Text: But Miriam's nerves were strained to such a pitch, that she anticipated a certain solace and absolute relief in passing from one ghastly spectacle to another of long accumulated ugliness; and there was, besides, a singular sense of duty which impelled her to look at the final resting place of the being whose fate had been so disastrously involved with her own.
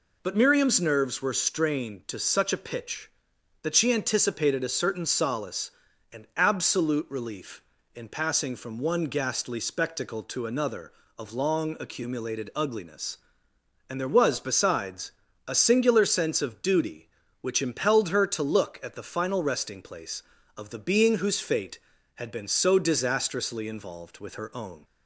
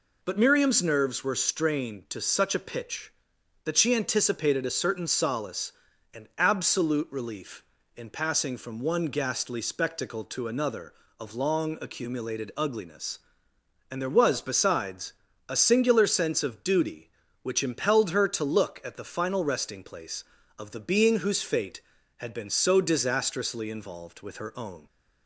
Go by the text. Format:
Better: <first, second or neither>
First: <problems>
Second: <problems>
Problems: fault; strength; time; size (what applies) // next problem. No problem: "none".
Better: neither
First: none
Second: none